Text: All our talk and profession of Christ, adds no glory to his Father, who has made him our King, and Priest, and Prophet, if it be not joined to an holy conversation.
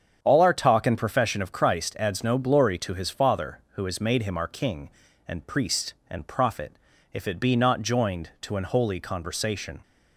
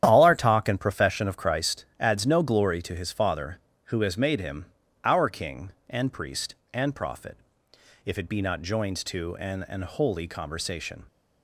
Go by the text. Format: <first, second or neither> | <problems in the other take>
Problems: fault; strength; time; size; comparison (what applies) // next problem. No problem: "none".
first | starts louder than the rest; strong; until 1.0 s; 10 dB; strong in the first // pauses between "him" and "our"; at 4.6 s; 0.40 s long // says "an" twice; at 9.6 s